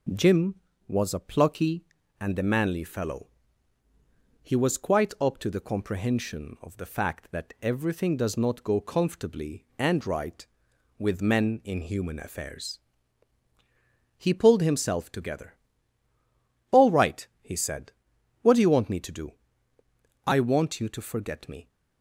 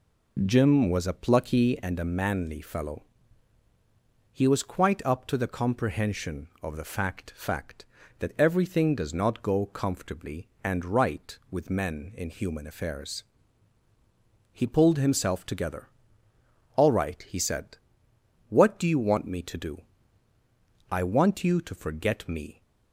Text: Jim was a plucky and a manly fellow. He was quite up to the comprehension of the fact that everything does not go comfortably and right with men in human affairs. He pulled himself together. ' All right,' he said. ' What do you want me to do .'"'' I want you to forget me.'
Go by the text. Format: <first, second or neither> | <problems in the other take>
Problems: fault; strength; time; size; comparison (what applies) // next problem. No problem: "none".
first | says "fact" twice; at 7.3 s